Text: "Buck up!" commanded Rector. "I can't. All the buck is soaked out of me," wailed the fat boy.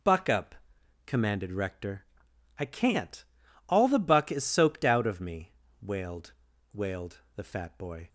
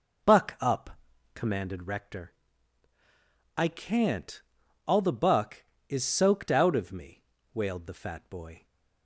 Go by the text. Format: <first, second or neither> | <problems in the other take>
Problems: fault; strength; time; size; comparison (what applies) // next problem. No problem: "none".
second | says "wailed" twice; at 6.7 s